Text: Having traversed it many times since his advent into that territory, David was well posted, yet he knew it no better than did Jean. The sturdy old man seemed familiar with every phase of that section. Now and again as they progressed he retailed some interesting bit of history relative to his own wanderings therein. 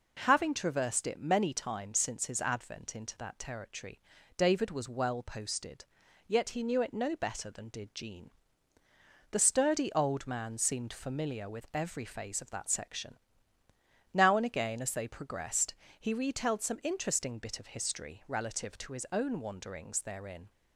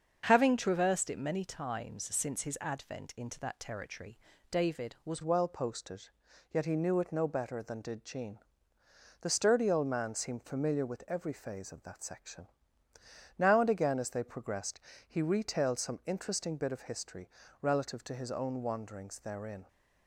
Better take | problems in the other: first | starts louder than the rest; until 1.2 s; 6.5 dB // changes voice at "well"; from 5.2 s on; 14.4 s long // pauses between "progressed" and "he"; slight; at 14.8 s; 0.26 s long; slight in the first // pauses between "history" and "relative"; slight; at 17.2 s; 0.32 s long

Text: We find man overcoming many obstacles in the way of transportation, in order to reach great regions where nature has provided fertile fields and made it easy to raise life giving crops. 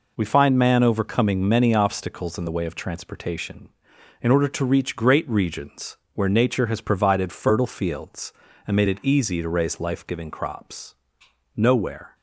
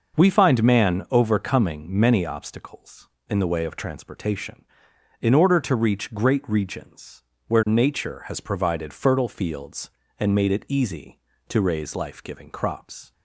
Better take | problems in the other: second | pauses between "regions" and "where"; slight; at 5.9 s; 0.16 s long; slight in the second // goes on to say "Nowhere"; from 11.5 s on; 0.60 s long

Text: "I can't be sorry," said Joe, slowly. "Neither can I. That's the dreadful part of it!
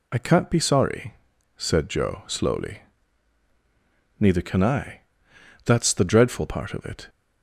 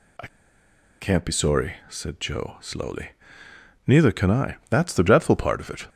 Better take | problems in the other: first | pauses between "I" and "can't"; noticeable; at 0.2 s; 0.72 s long

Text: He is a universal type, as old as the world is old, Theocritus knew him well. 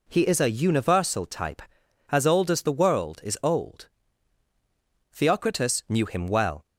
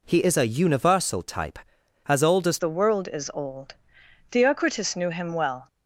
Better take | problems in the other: first | changes voice at "the"; from 2.5 s on; 3.1 s long

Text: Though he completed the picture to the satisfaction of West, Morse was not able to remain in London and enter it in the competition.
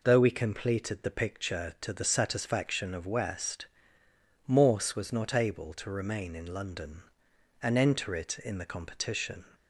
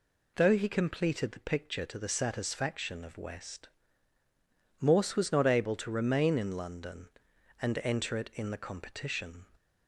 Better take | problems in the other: second | says "we" for "he"; at 0.1 s

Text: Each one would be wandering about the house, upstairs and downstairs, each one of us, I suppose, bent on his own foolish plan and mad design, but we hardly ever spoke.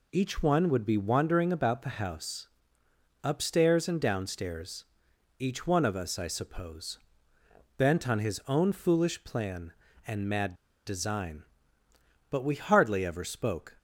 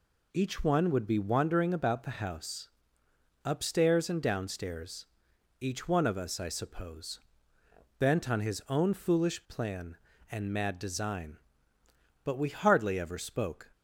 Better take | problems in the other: second | pauses between "mad" and "design"; slight; at 10.5 s; 0.32 s long

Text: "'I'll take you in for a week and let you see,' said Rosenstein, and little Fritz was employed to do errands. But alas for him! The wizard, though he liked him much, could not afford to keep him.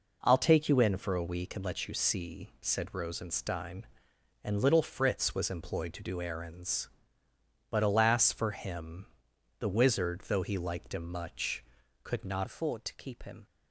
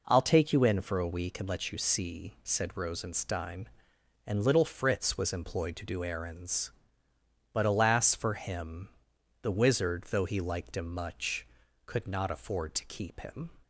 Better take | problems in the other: second | changes voice at "afford"; from 12.4 s on; 1.0 s long

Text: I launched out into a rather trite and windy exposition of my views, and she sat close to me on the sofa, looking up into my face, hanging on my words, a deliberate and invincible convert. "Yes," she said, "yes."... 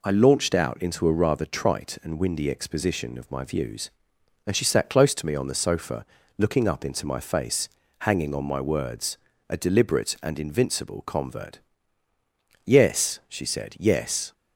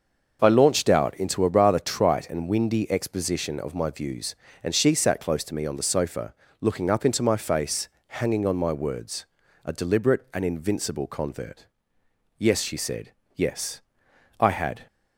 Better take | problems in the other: first | starts louder than the rest; until 1.4 s; 6.5 dB // goes on to say "I had"; slight; from 14.3 s on; 0.48 s long

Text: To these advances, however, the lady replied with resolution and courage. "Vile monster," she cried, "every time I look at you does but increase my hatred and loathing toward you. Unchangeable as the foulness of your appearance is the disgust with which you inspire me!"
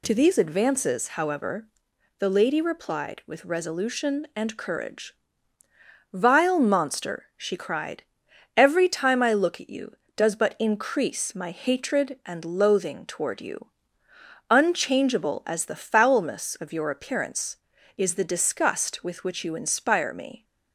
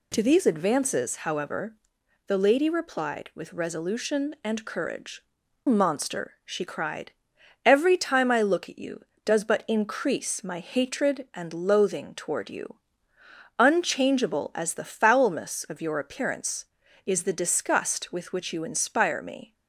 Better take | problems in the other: first | skips "Vile"; at 5.4 s

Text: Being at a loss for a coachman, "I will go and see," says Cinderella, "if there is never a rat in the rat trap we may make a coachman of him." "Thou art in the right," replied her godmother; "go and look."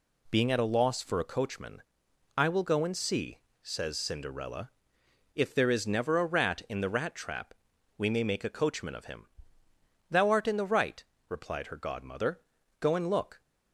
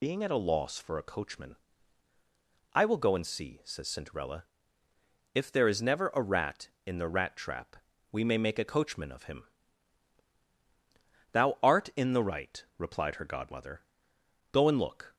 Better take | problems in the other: first | loses the start of "Being"; at 0.0 s; 40 ms // pauses between "trap" and "we"; slight; at 7.7 s; 0.36 s long; also in the first

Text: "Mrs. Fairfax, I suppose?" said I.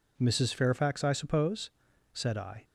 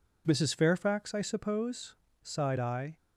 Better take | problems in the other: first | says "sighed" for "said"; at 2.2 s

